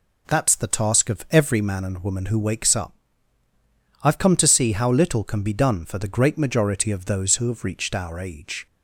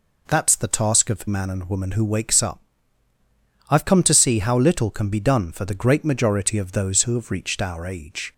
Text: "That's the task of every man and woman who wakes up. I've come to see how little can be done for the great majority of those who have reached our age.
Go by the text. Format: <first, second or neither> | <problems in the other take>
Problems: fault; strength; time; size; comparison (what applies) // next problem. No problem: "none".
first | skips "every"; at 1.2 s